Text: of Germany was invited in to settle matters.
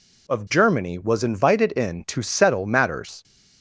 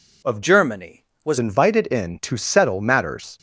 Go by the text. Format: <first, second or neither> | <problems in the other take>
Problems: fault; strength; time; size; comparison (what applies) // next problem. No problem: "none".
first | changes voice from "Germany" to "was"; from 0.4 to 1.3 s; 0.9 s long